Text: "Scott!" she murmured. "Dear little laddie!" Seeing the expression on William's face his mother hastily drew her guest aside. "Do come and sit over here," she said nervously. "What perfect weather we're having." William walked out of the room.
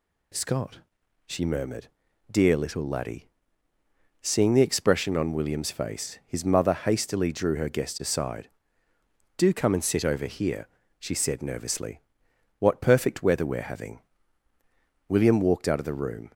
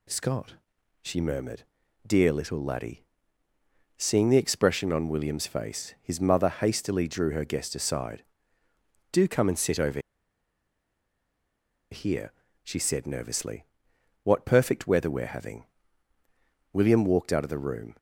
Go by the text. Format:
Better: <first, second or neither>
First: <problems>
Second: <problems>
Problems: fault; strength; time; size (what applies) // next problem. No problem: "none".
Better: first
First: none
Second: pauses between "over" and "here"; strong; at 10.0 s; 1.9 s long